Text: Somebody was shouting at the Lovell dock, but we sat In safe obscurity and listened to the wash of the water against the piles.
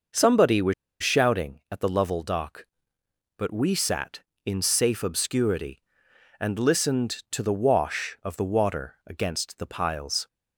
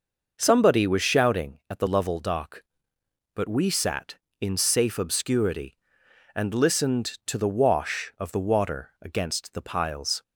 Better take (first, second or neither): second